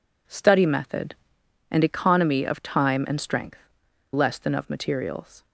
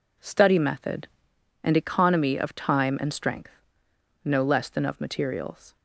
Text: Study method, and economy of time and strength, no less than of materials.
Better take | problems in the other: second | skips "no"; at 3.8 s

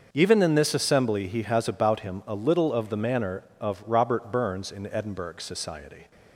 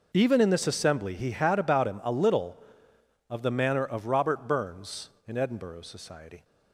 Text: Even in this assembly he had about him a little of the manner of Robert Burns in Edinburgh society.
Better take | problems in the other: second | starts louder than the rest; until 1.1 s; 6.5 dB // says "has" for "had"; at 1.4 s

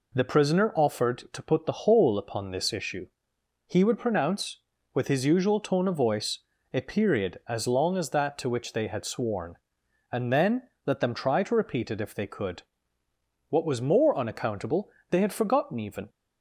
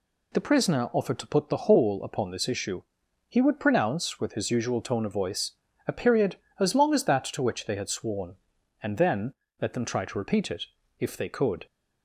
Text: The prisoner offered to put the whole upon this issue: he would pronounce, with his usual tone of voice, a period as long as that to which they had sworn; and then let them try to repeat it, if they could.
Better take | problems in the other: second | pauses between "then" and "let"; slight; at 10.6 s; 0.16 s long; slight in the second // goes on to say "What was more unaccountable they had forgotten even"; strong; from 13.4 s on; 2.6 s long

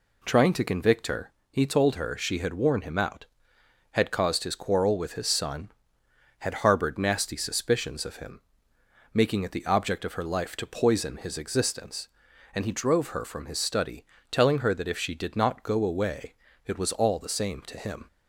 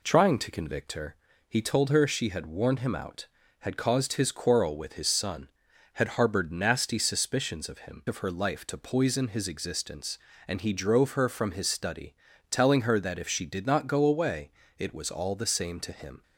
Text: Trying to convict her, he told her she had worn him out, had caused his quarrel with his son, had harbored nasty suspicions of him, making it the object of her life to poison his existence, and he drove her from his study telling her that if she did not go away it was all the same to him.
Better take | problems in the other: first | skips "making it the object"; at 8.0 s // pauses between "study" and "telling"; slight; at 12.1 s; 0.34 s long; slight in the first // pauses between "away" and "it"; slight; at 14.5 s; 0.26 s long; slight in the first

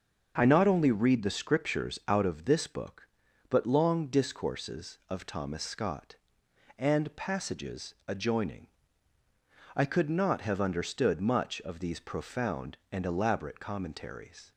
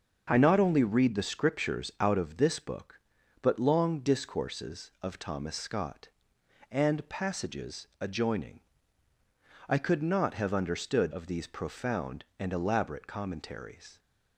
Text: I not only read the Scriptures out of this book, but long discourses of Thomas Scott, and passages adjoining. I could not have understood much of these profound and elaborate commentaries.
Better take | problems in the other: first | starts louder than the rest; until 1.3 s; 6.5 dB; also in the first // skips "much"; at 11.1 s

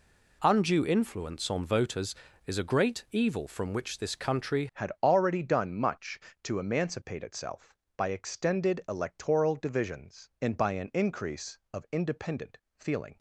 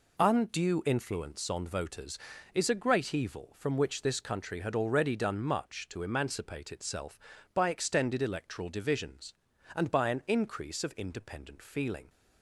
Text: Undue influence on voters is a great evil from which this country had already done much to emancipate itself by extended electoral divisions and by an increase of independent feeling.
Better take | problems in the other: second | changes voice at "had"; from 4.7 s on; 8.4 s long // pauses between "independent" and "feeling"; slight; at 12.5 s; 0.18 s long

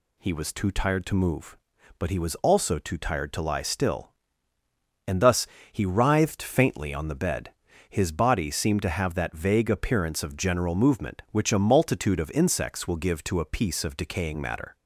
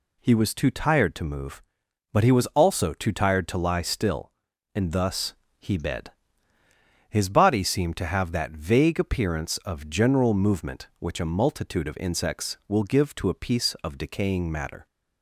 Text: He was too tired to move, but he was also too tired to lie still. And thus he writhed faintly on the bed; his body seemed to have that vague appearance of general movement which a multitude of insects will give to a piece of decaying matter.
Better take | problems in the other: first | pauses between "thus" and "he"; slight; at 5.3 s; 0.24 s long; slight in the first // skips "writhed faintly on the"; at 5.7 s

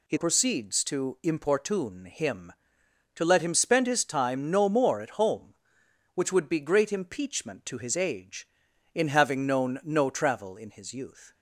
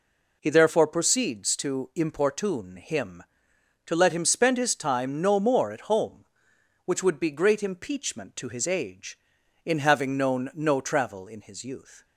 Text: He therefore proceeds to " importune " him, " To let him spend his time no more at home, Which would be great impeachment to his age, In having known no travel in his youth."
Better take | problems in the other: second | skips "therefore"; at 0.1 s

